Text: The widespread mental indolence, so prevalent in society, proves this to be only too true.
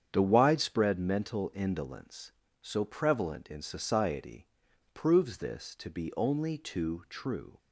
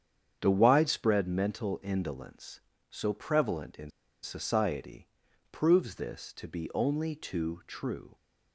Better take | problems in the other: first | starts louder than the rest; strong; until 1.4 s; 8 dB; strong in the first // pauses between "in" and "society"; slight; at 3.9 s; 0.32 s long

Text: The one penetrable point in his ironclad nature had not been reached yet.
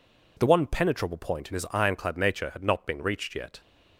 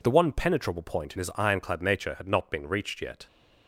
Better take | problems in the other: neither | none

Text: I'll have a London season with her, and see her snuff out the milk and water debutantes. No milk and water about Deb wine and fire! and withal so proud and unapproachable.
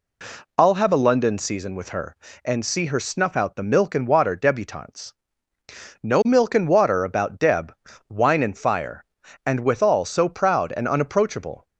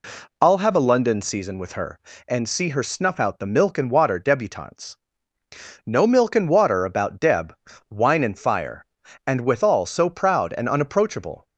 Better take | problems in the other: neither | pauses between "Deb" and "wine"; slight; the same in both

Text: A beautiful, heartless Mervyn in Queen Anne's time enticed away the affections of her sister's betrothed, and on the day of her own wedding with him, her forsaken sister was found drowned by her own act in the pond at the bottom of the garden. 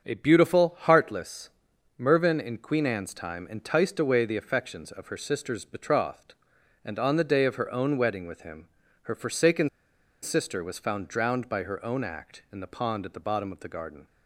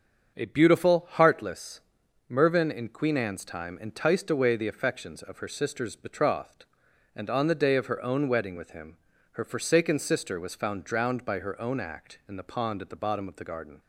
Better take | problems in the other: second | starts louder than the rest; strong; until 1.0 s; 7.5 dB; strong in the second // pauses between "heartless" and "Mervyn"; noticeable; at 1.4 s; 0.48 s long; noticeable in the second // pauses between "forsaken" and "sister"; noticeable; at 9.6 s; 0.53 s long

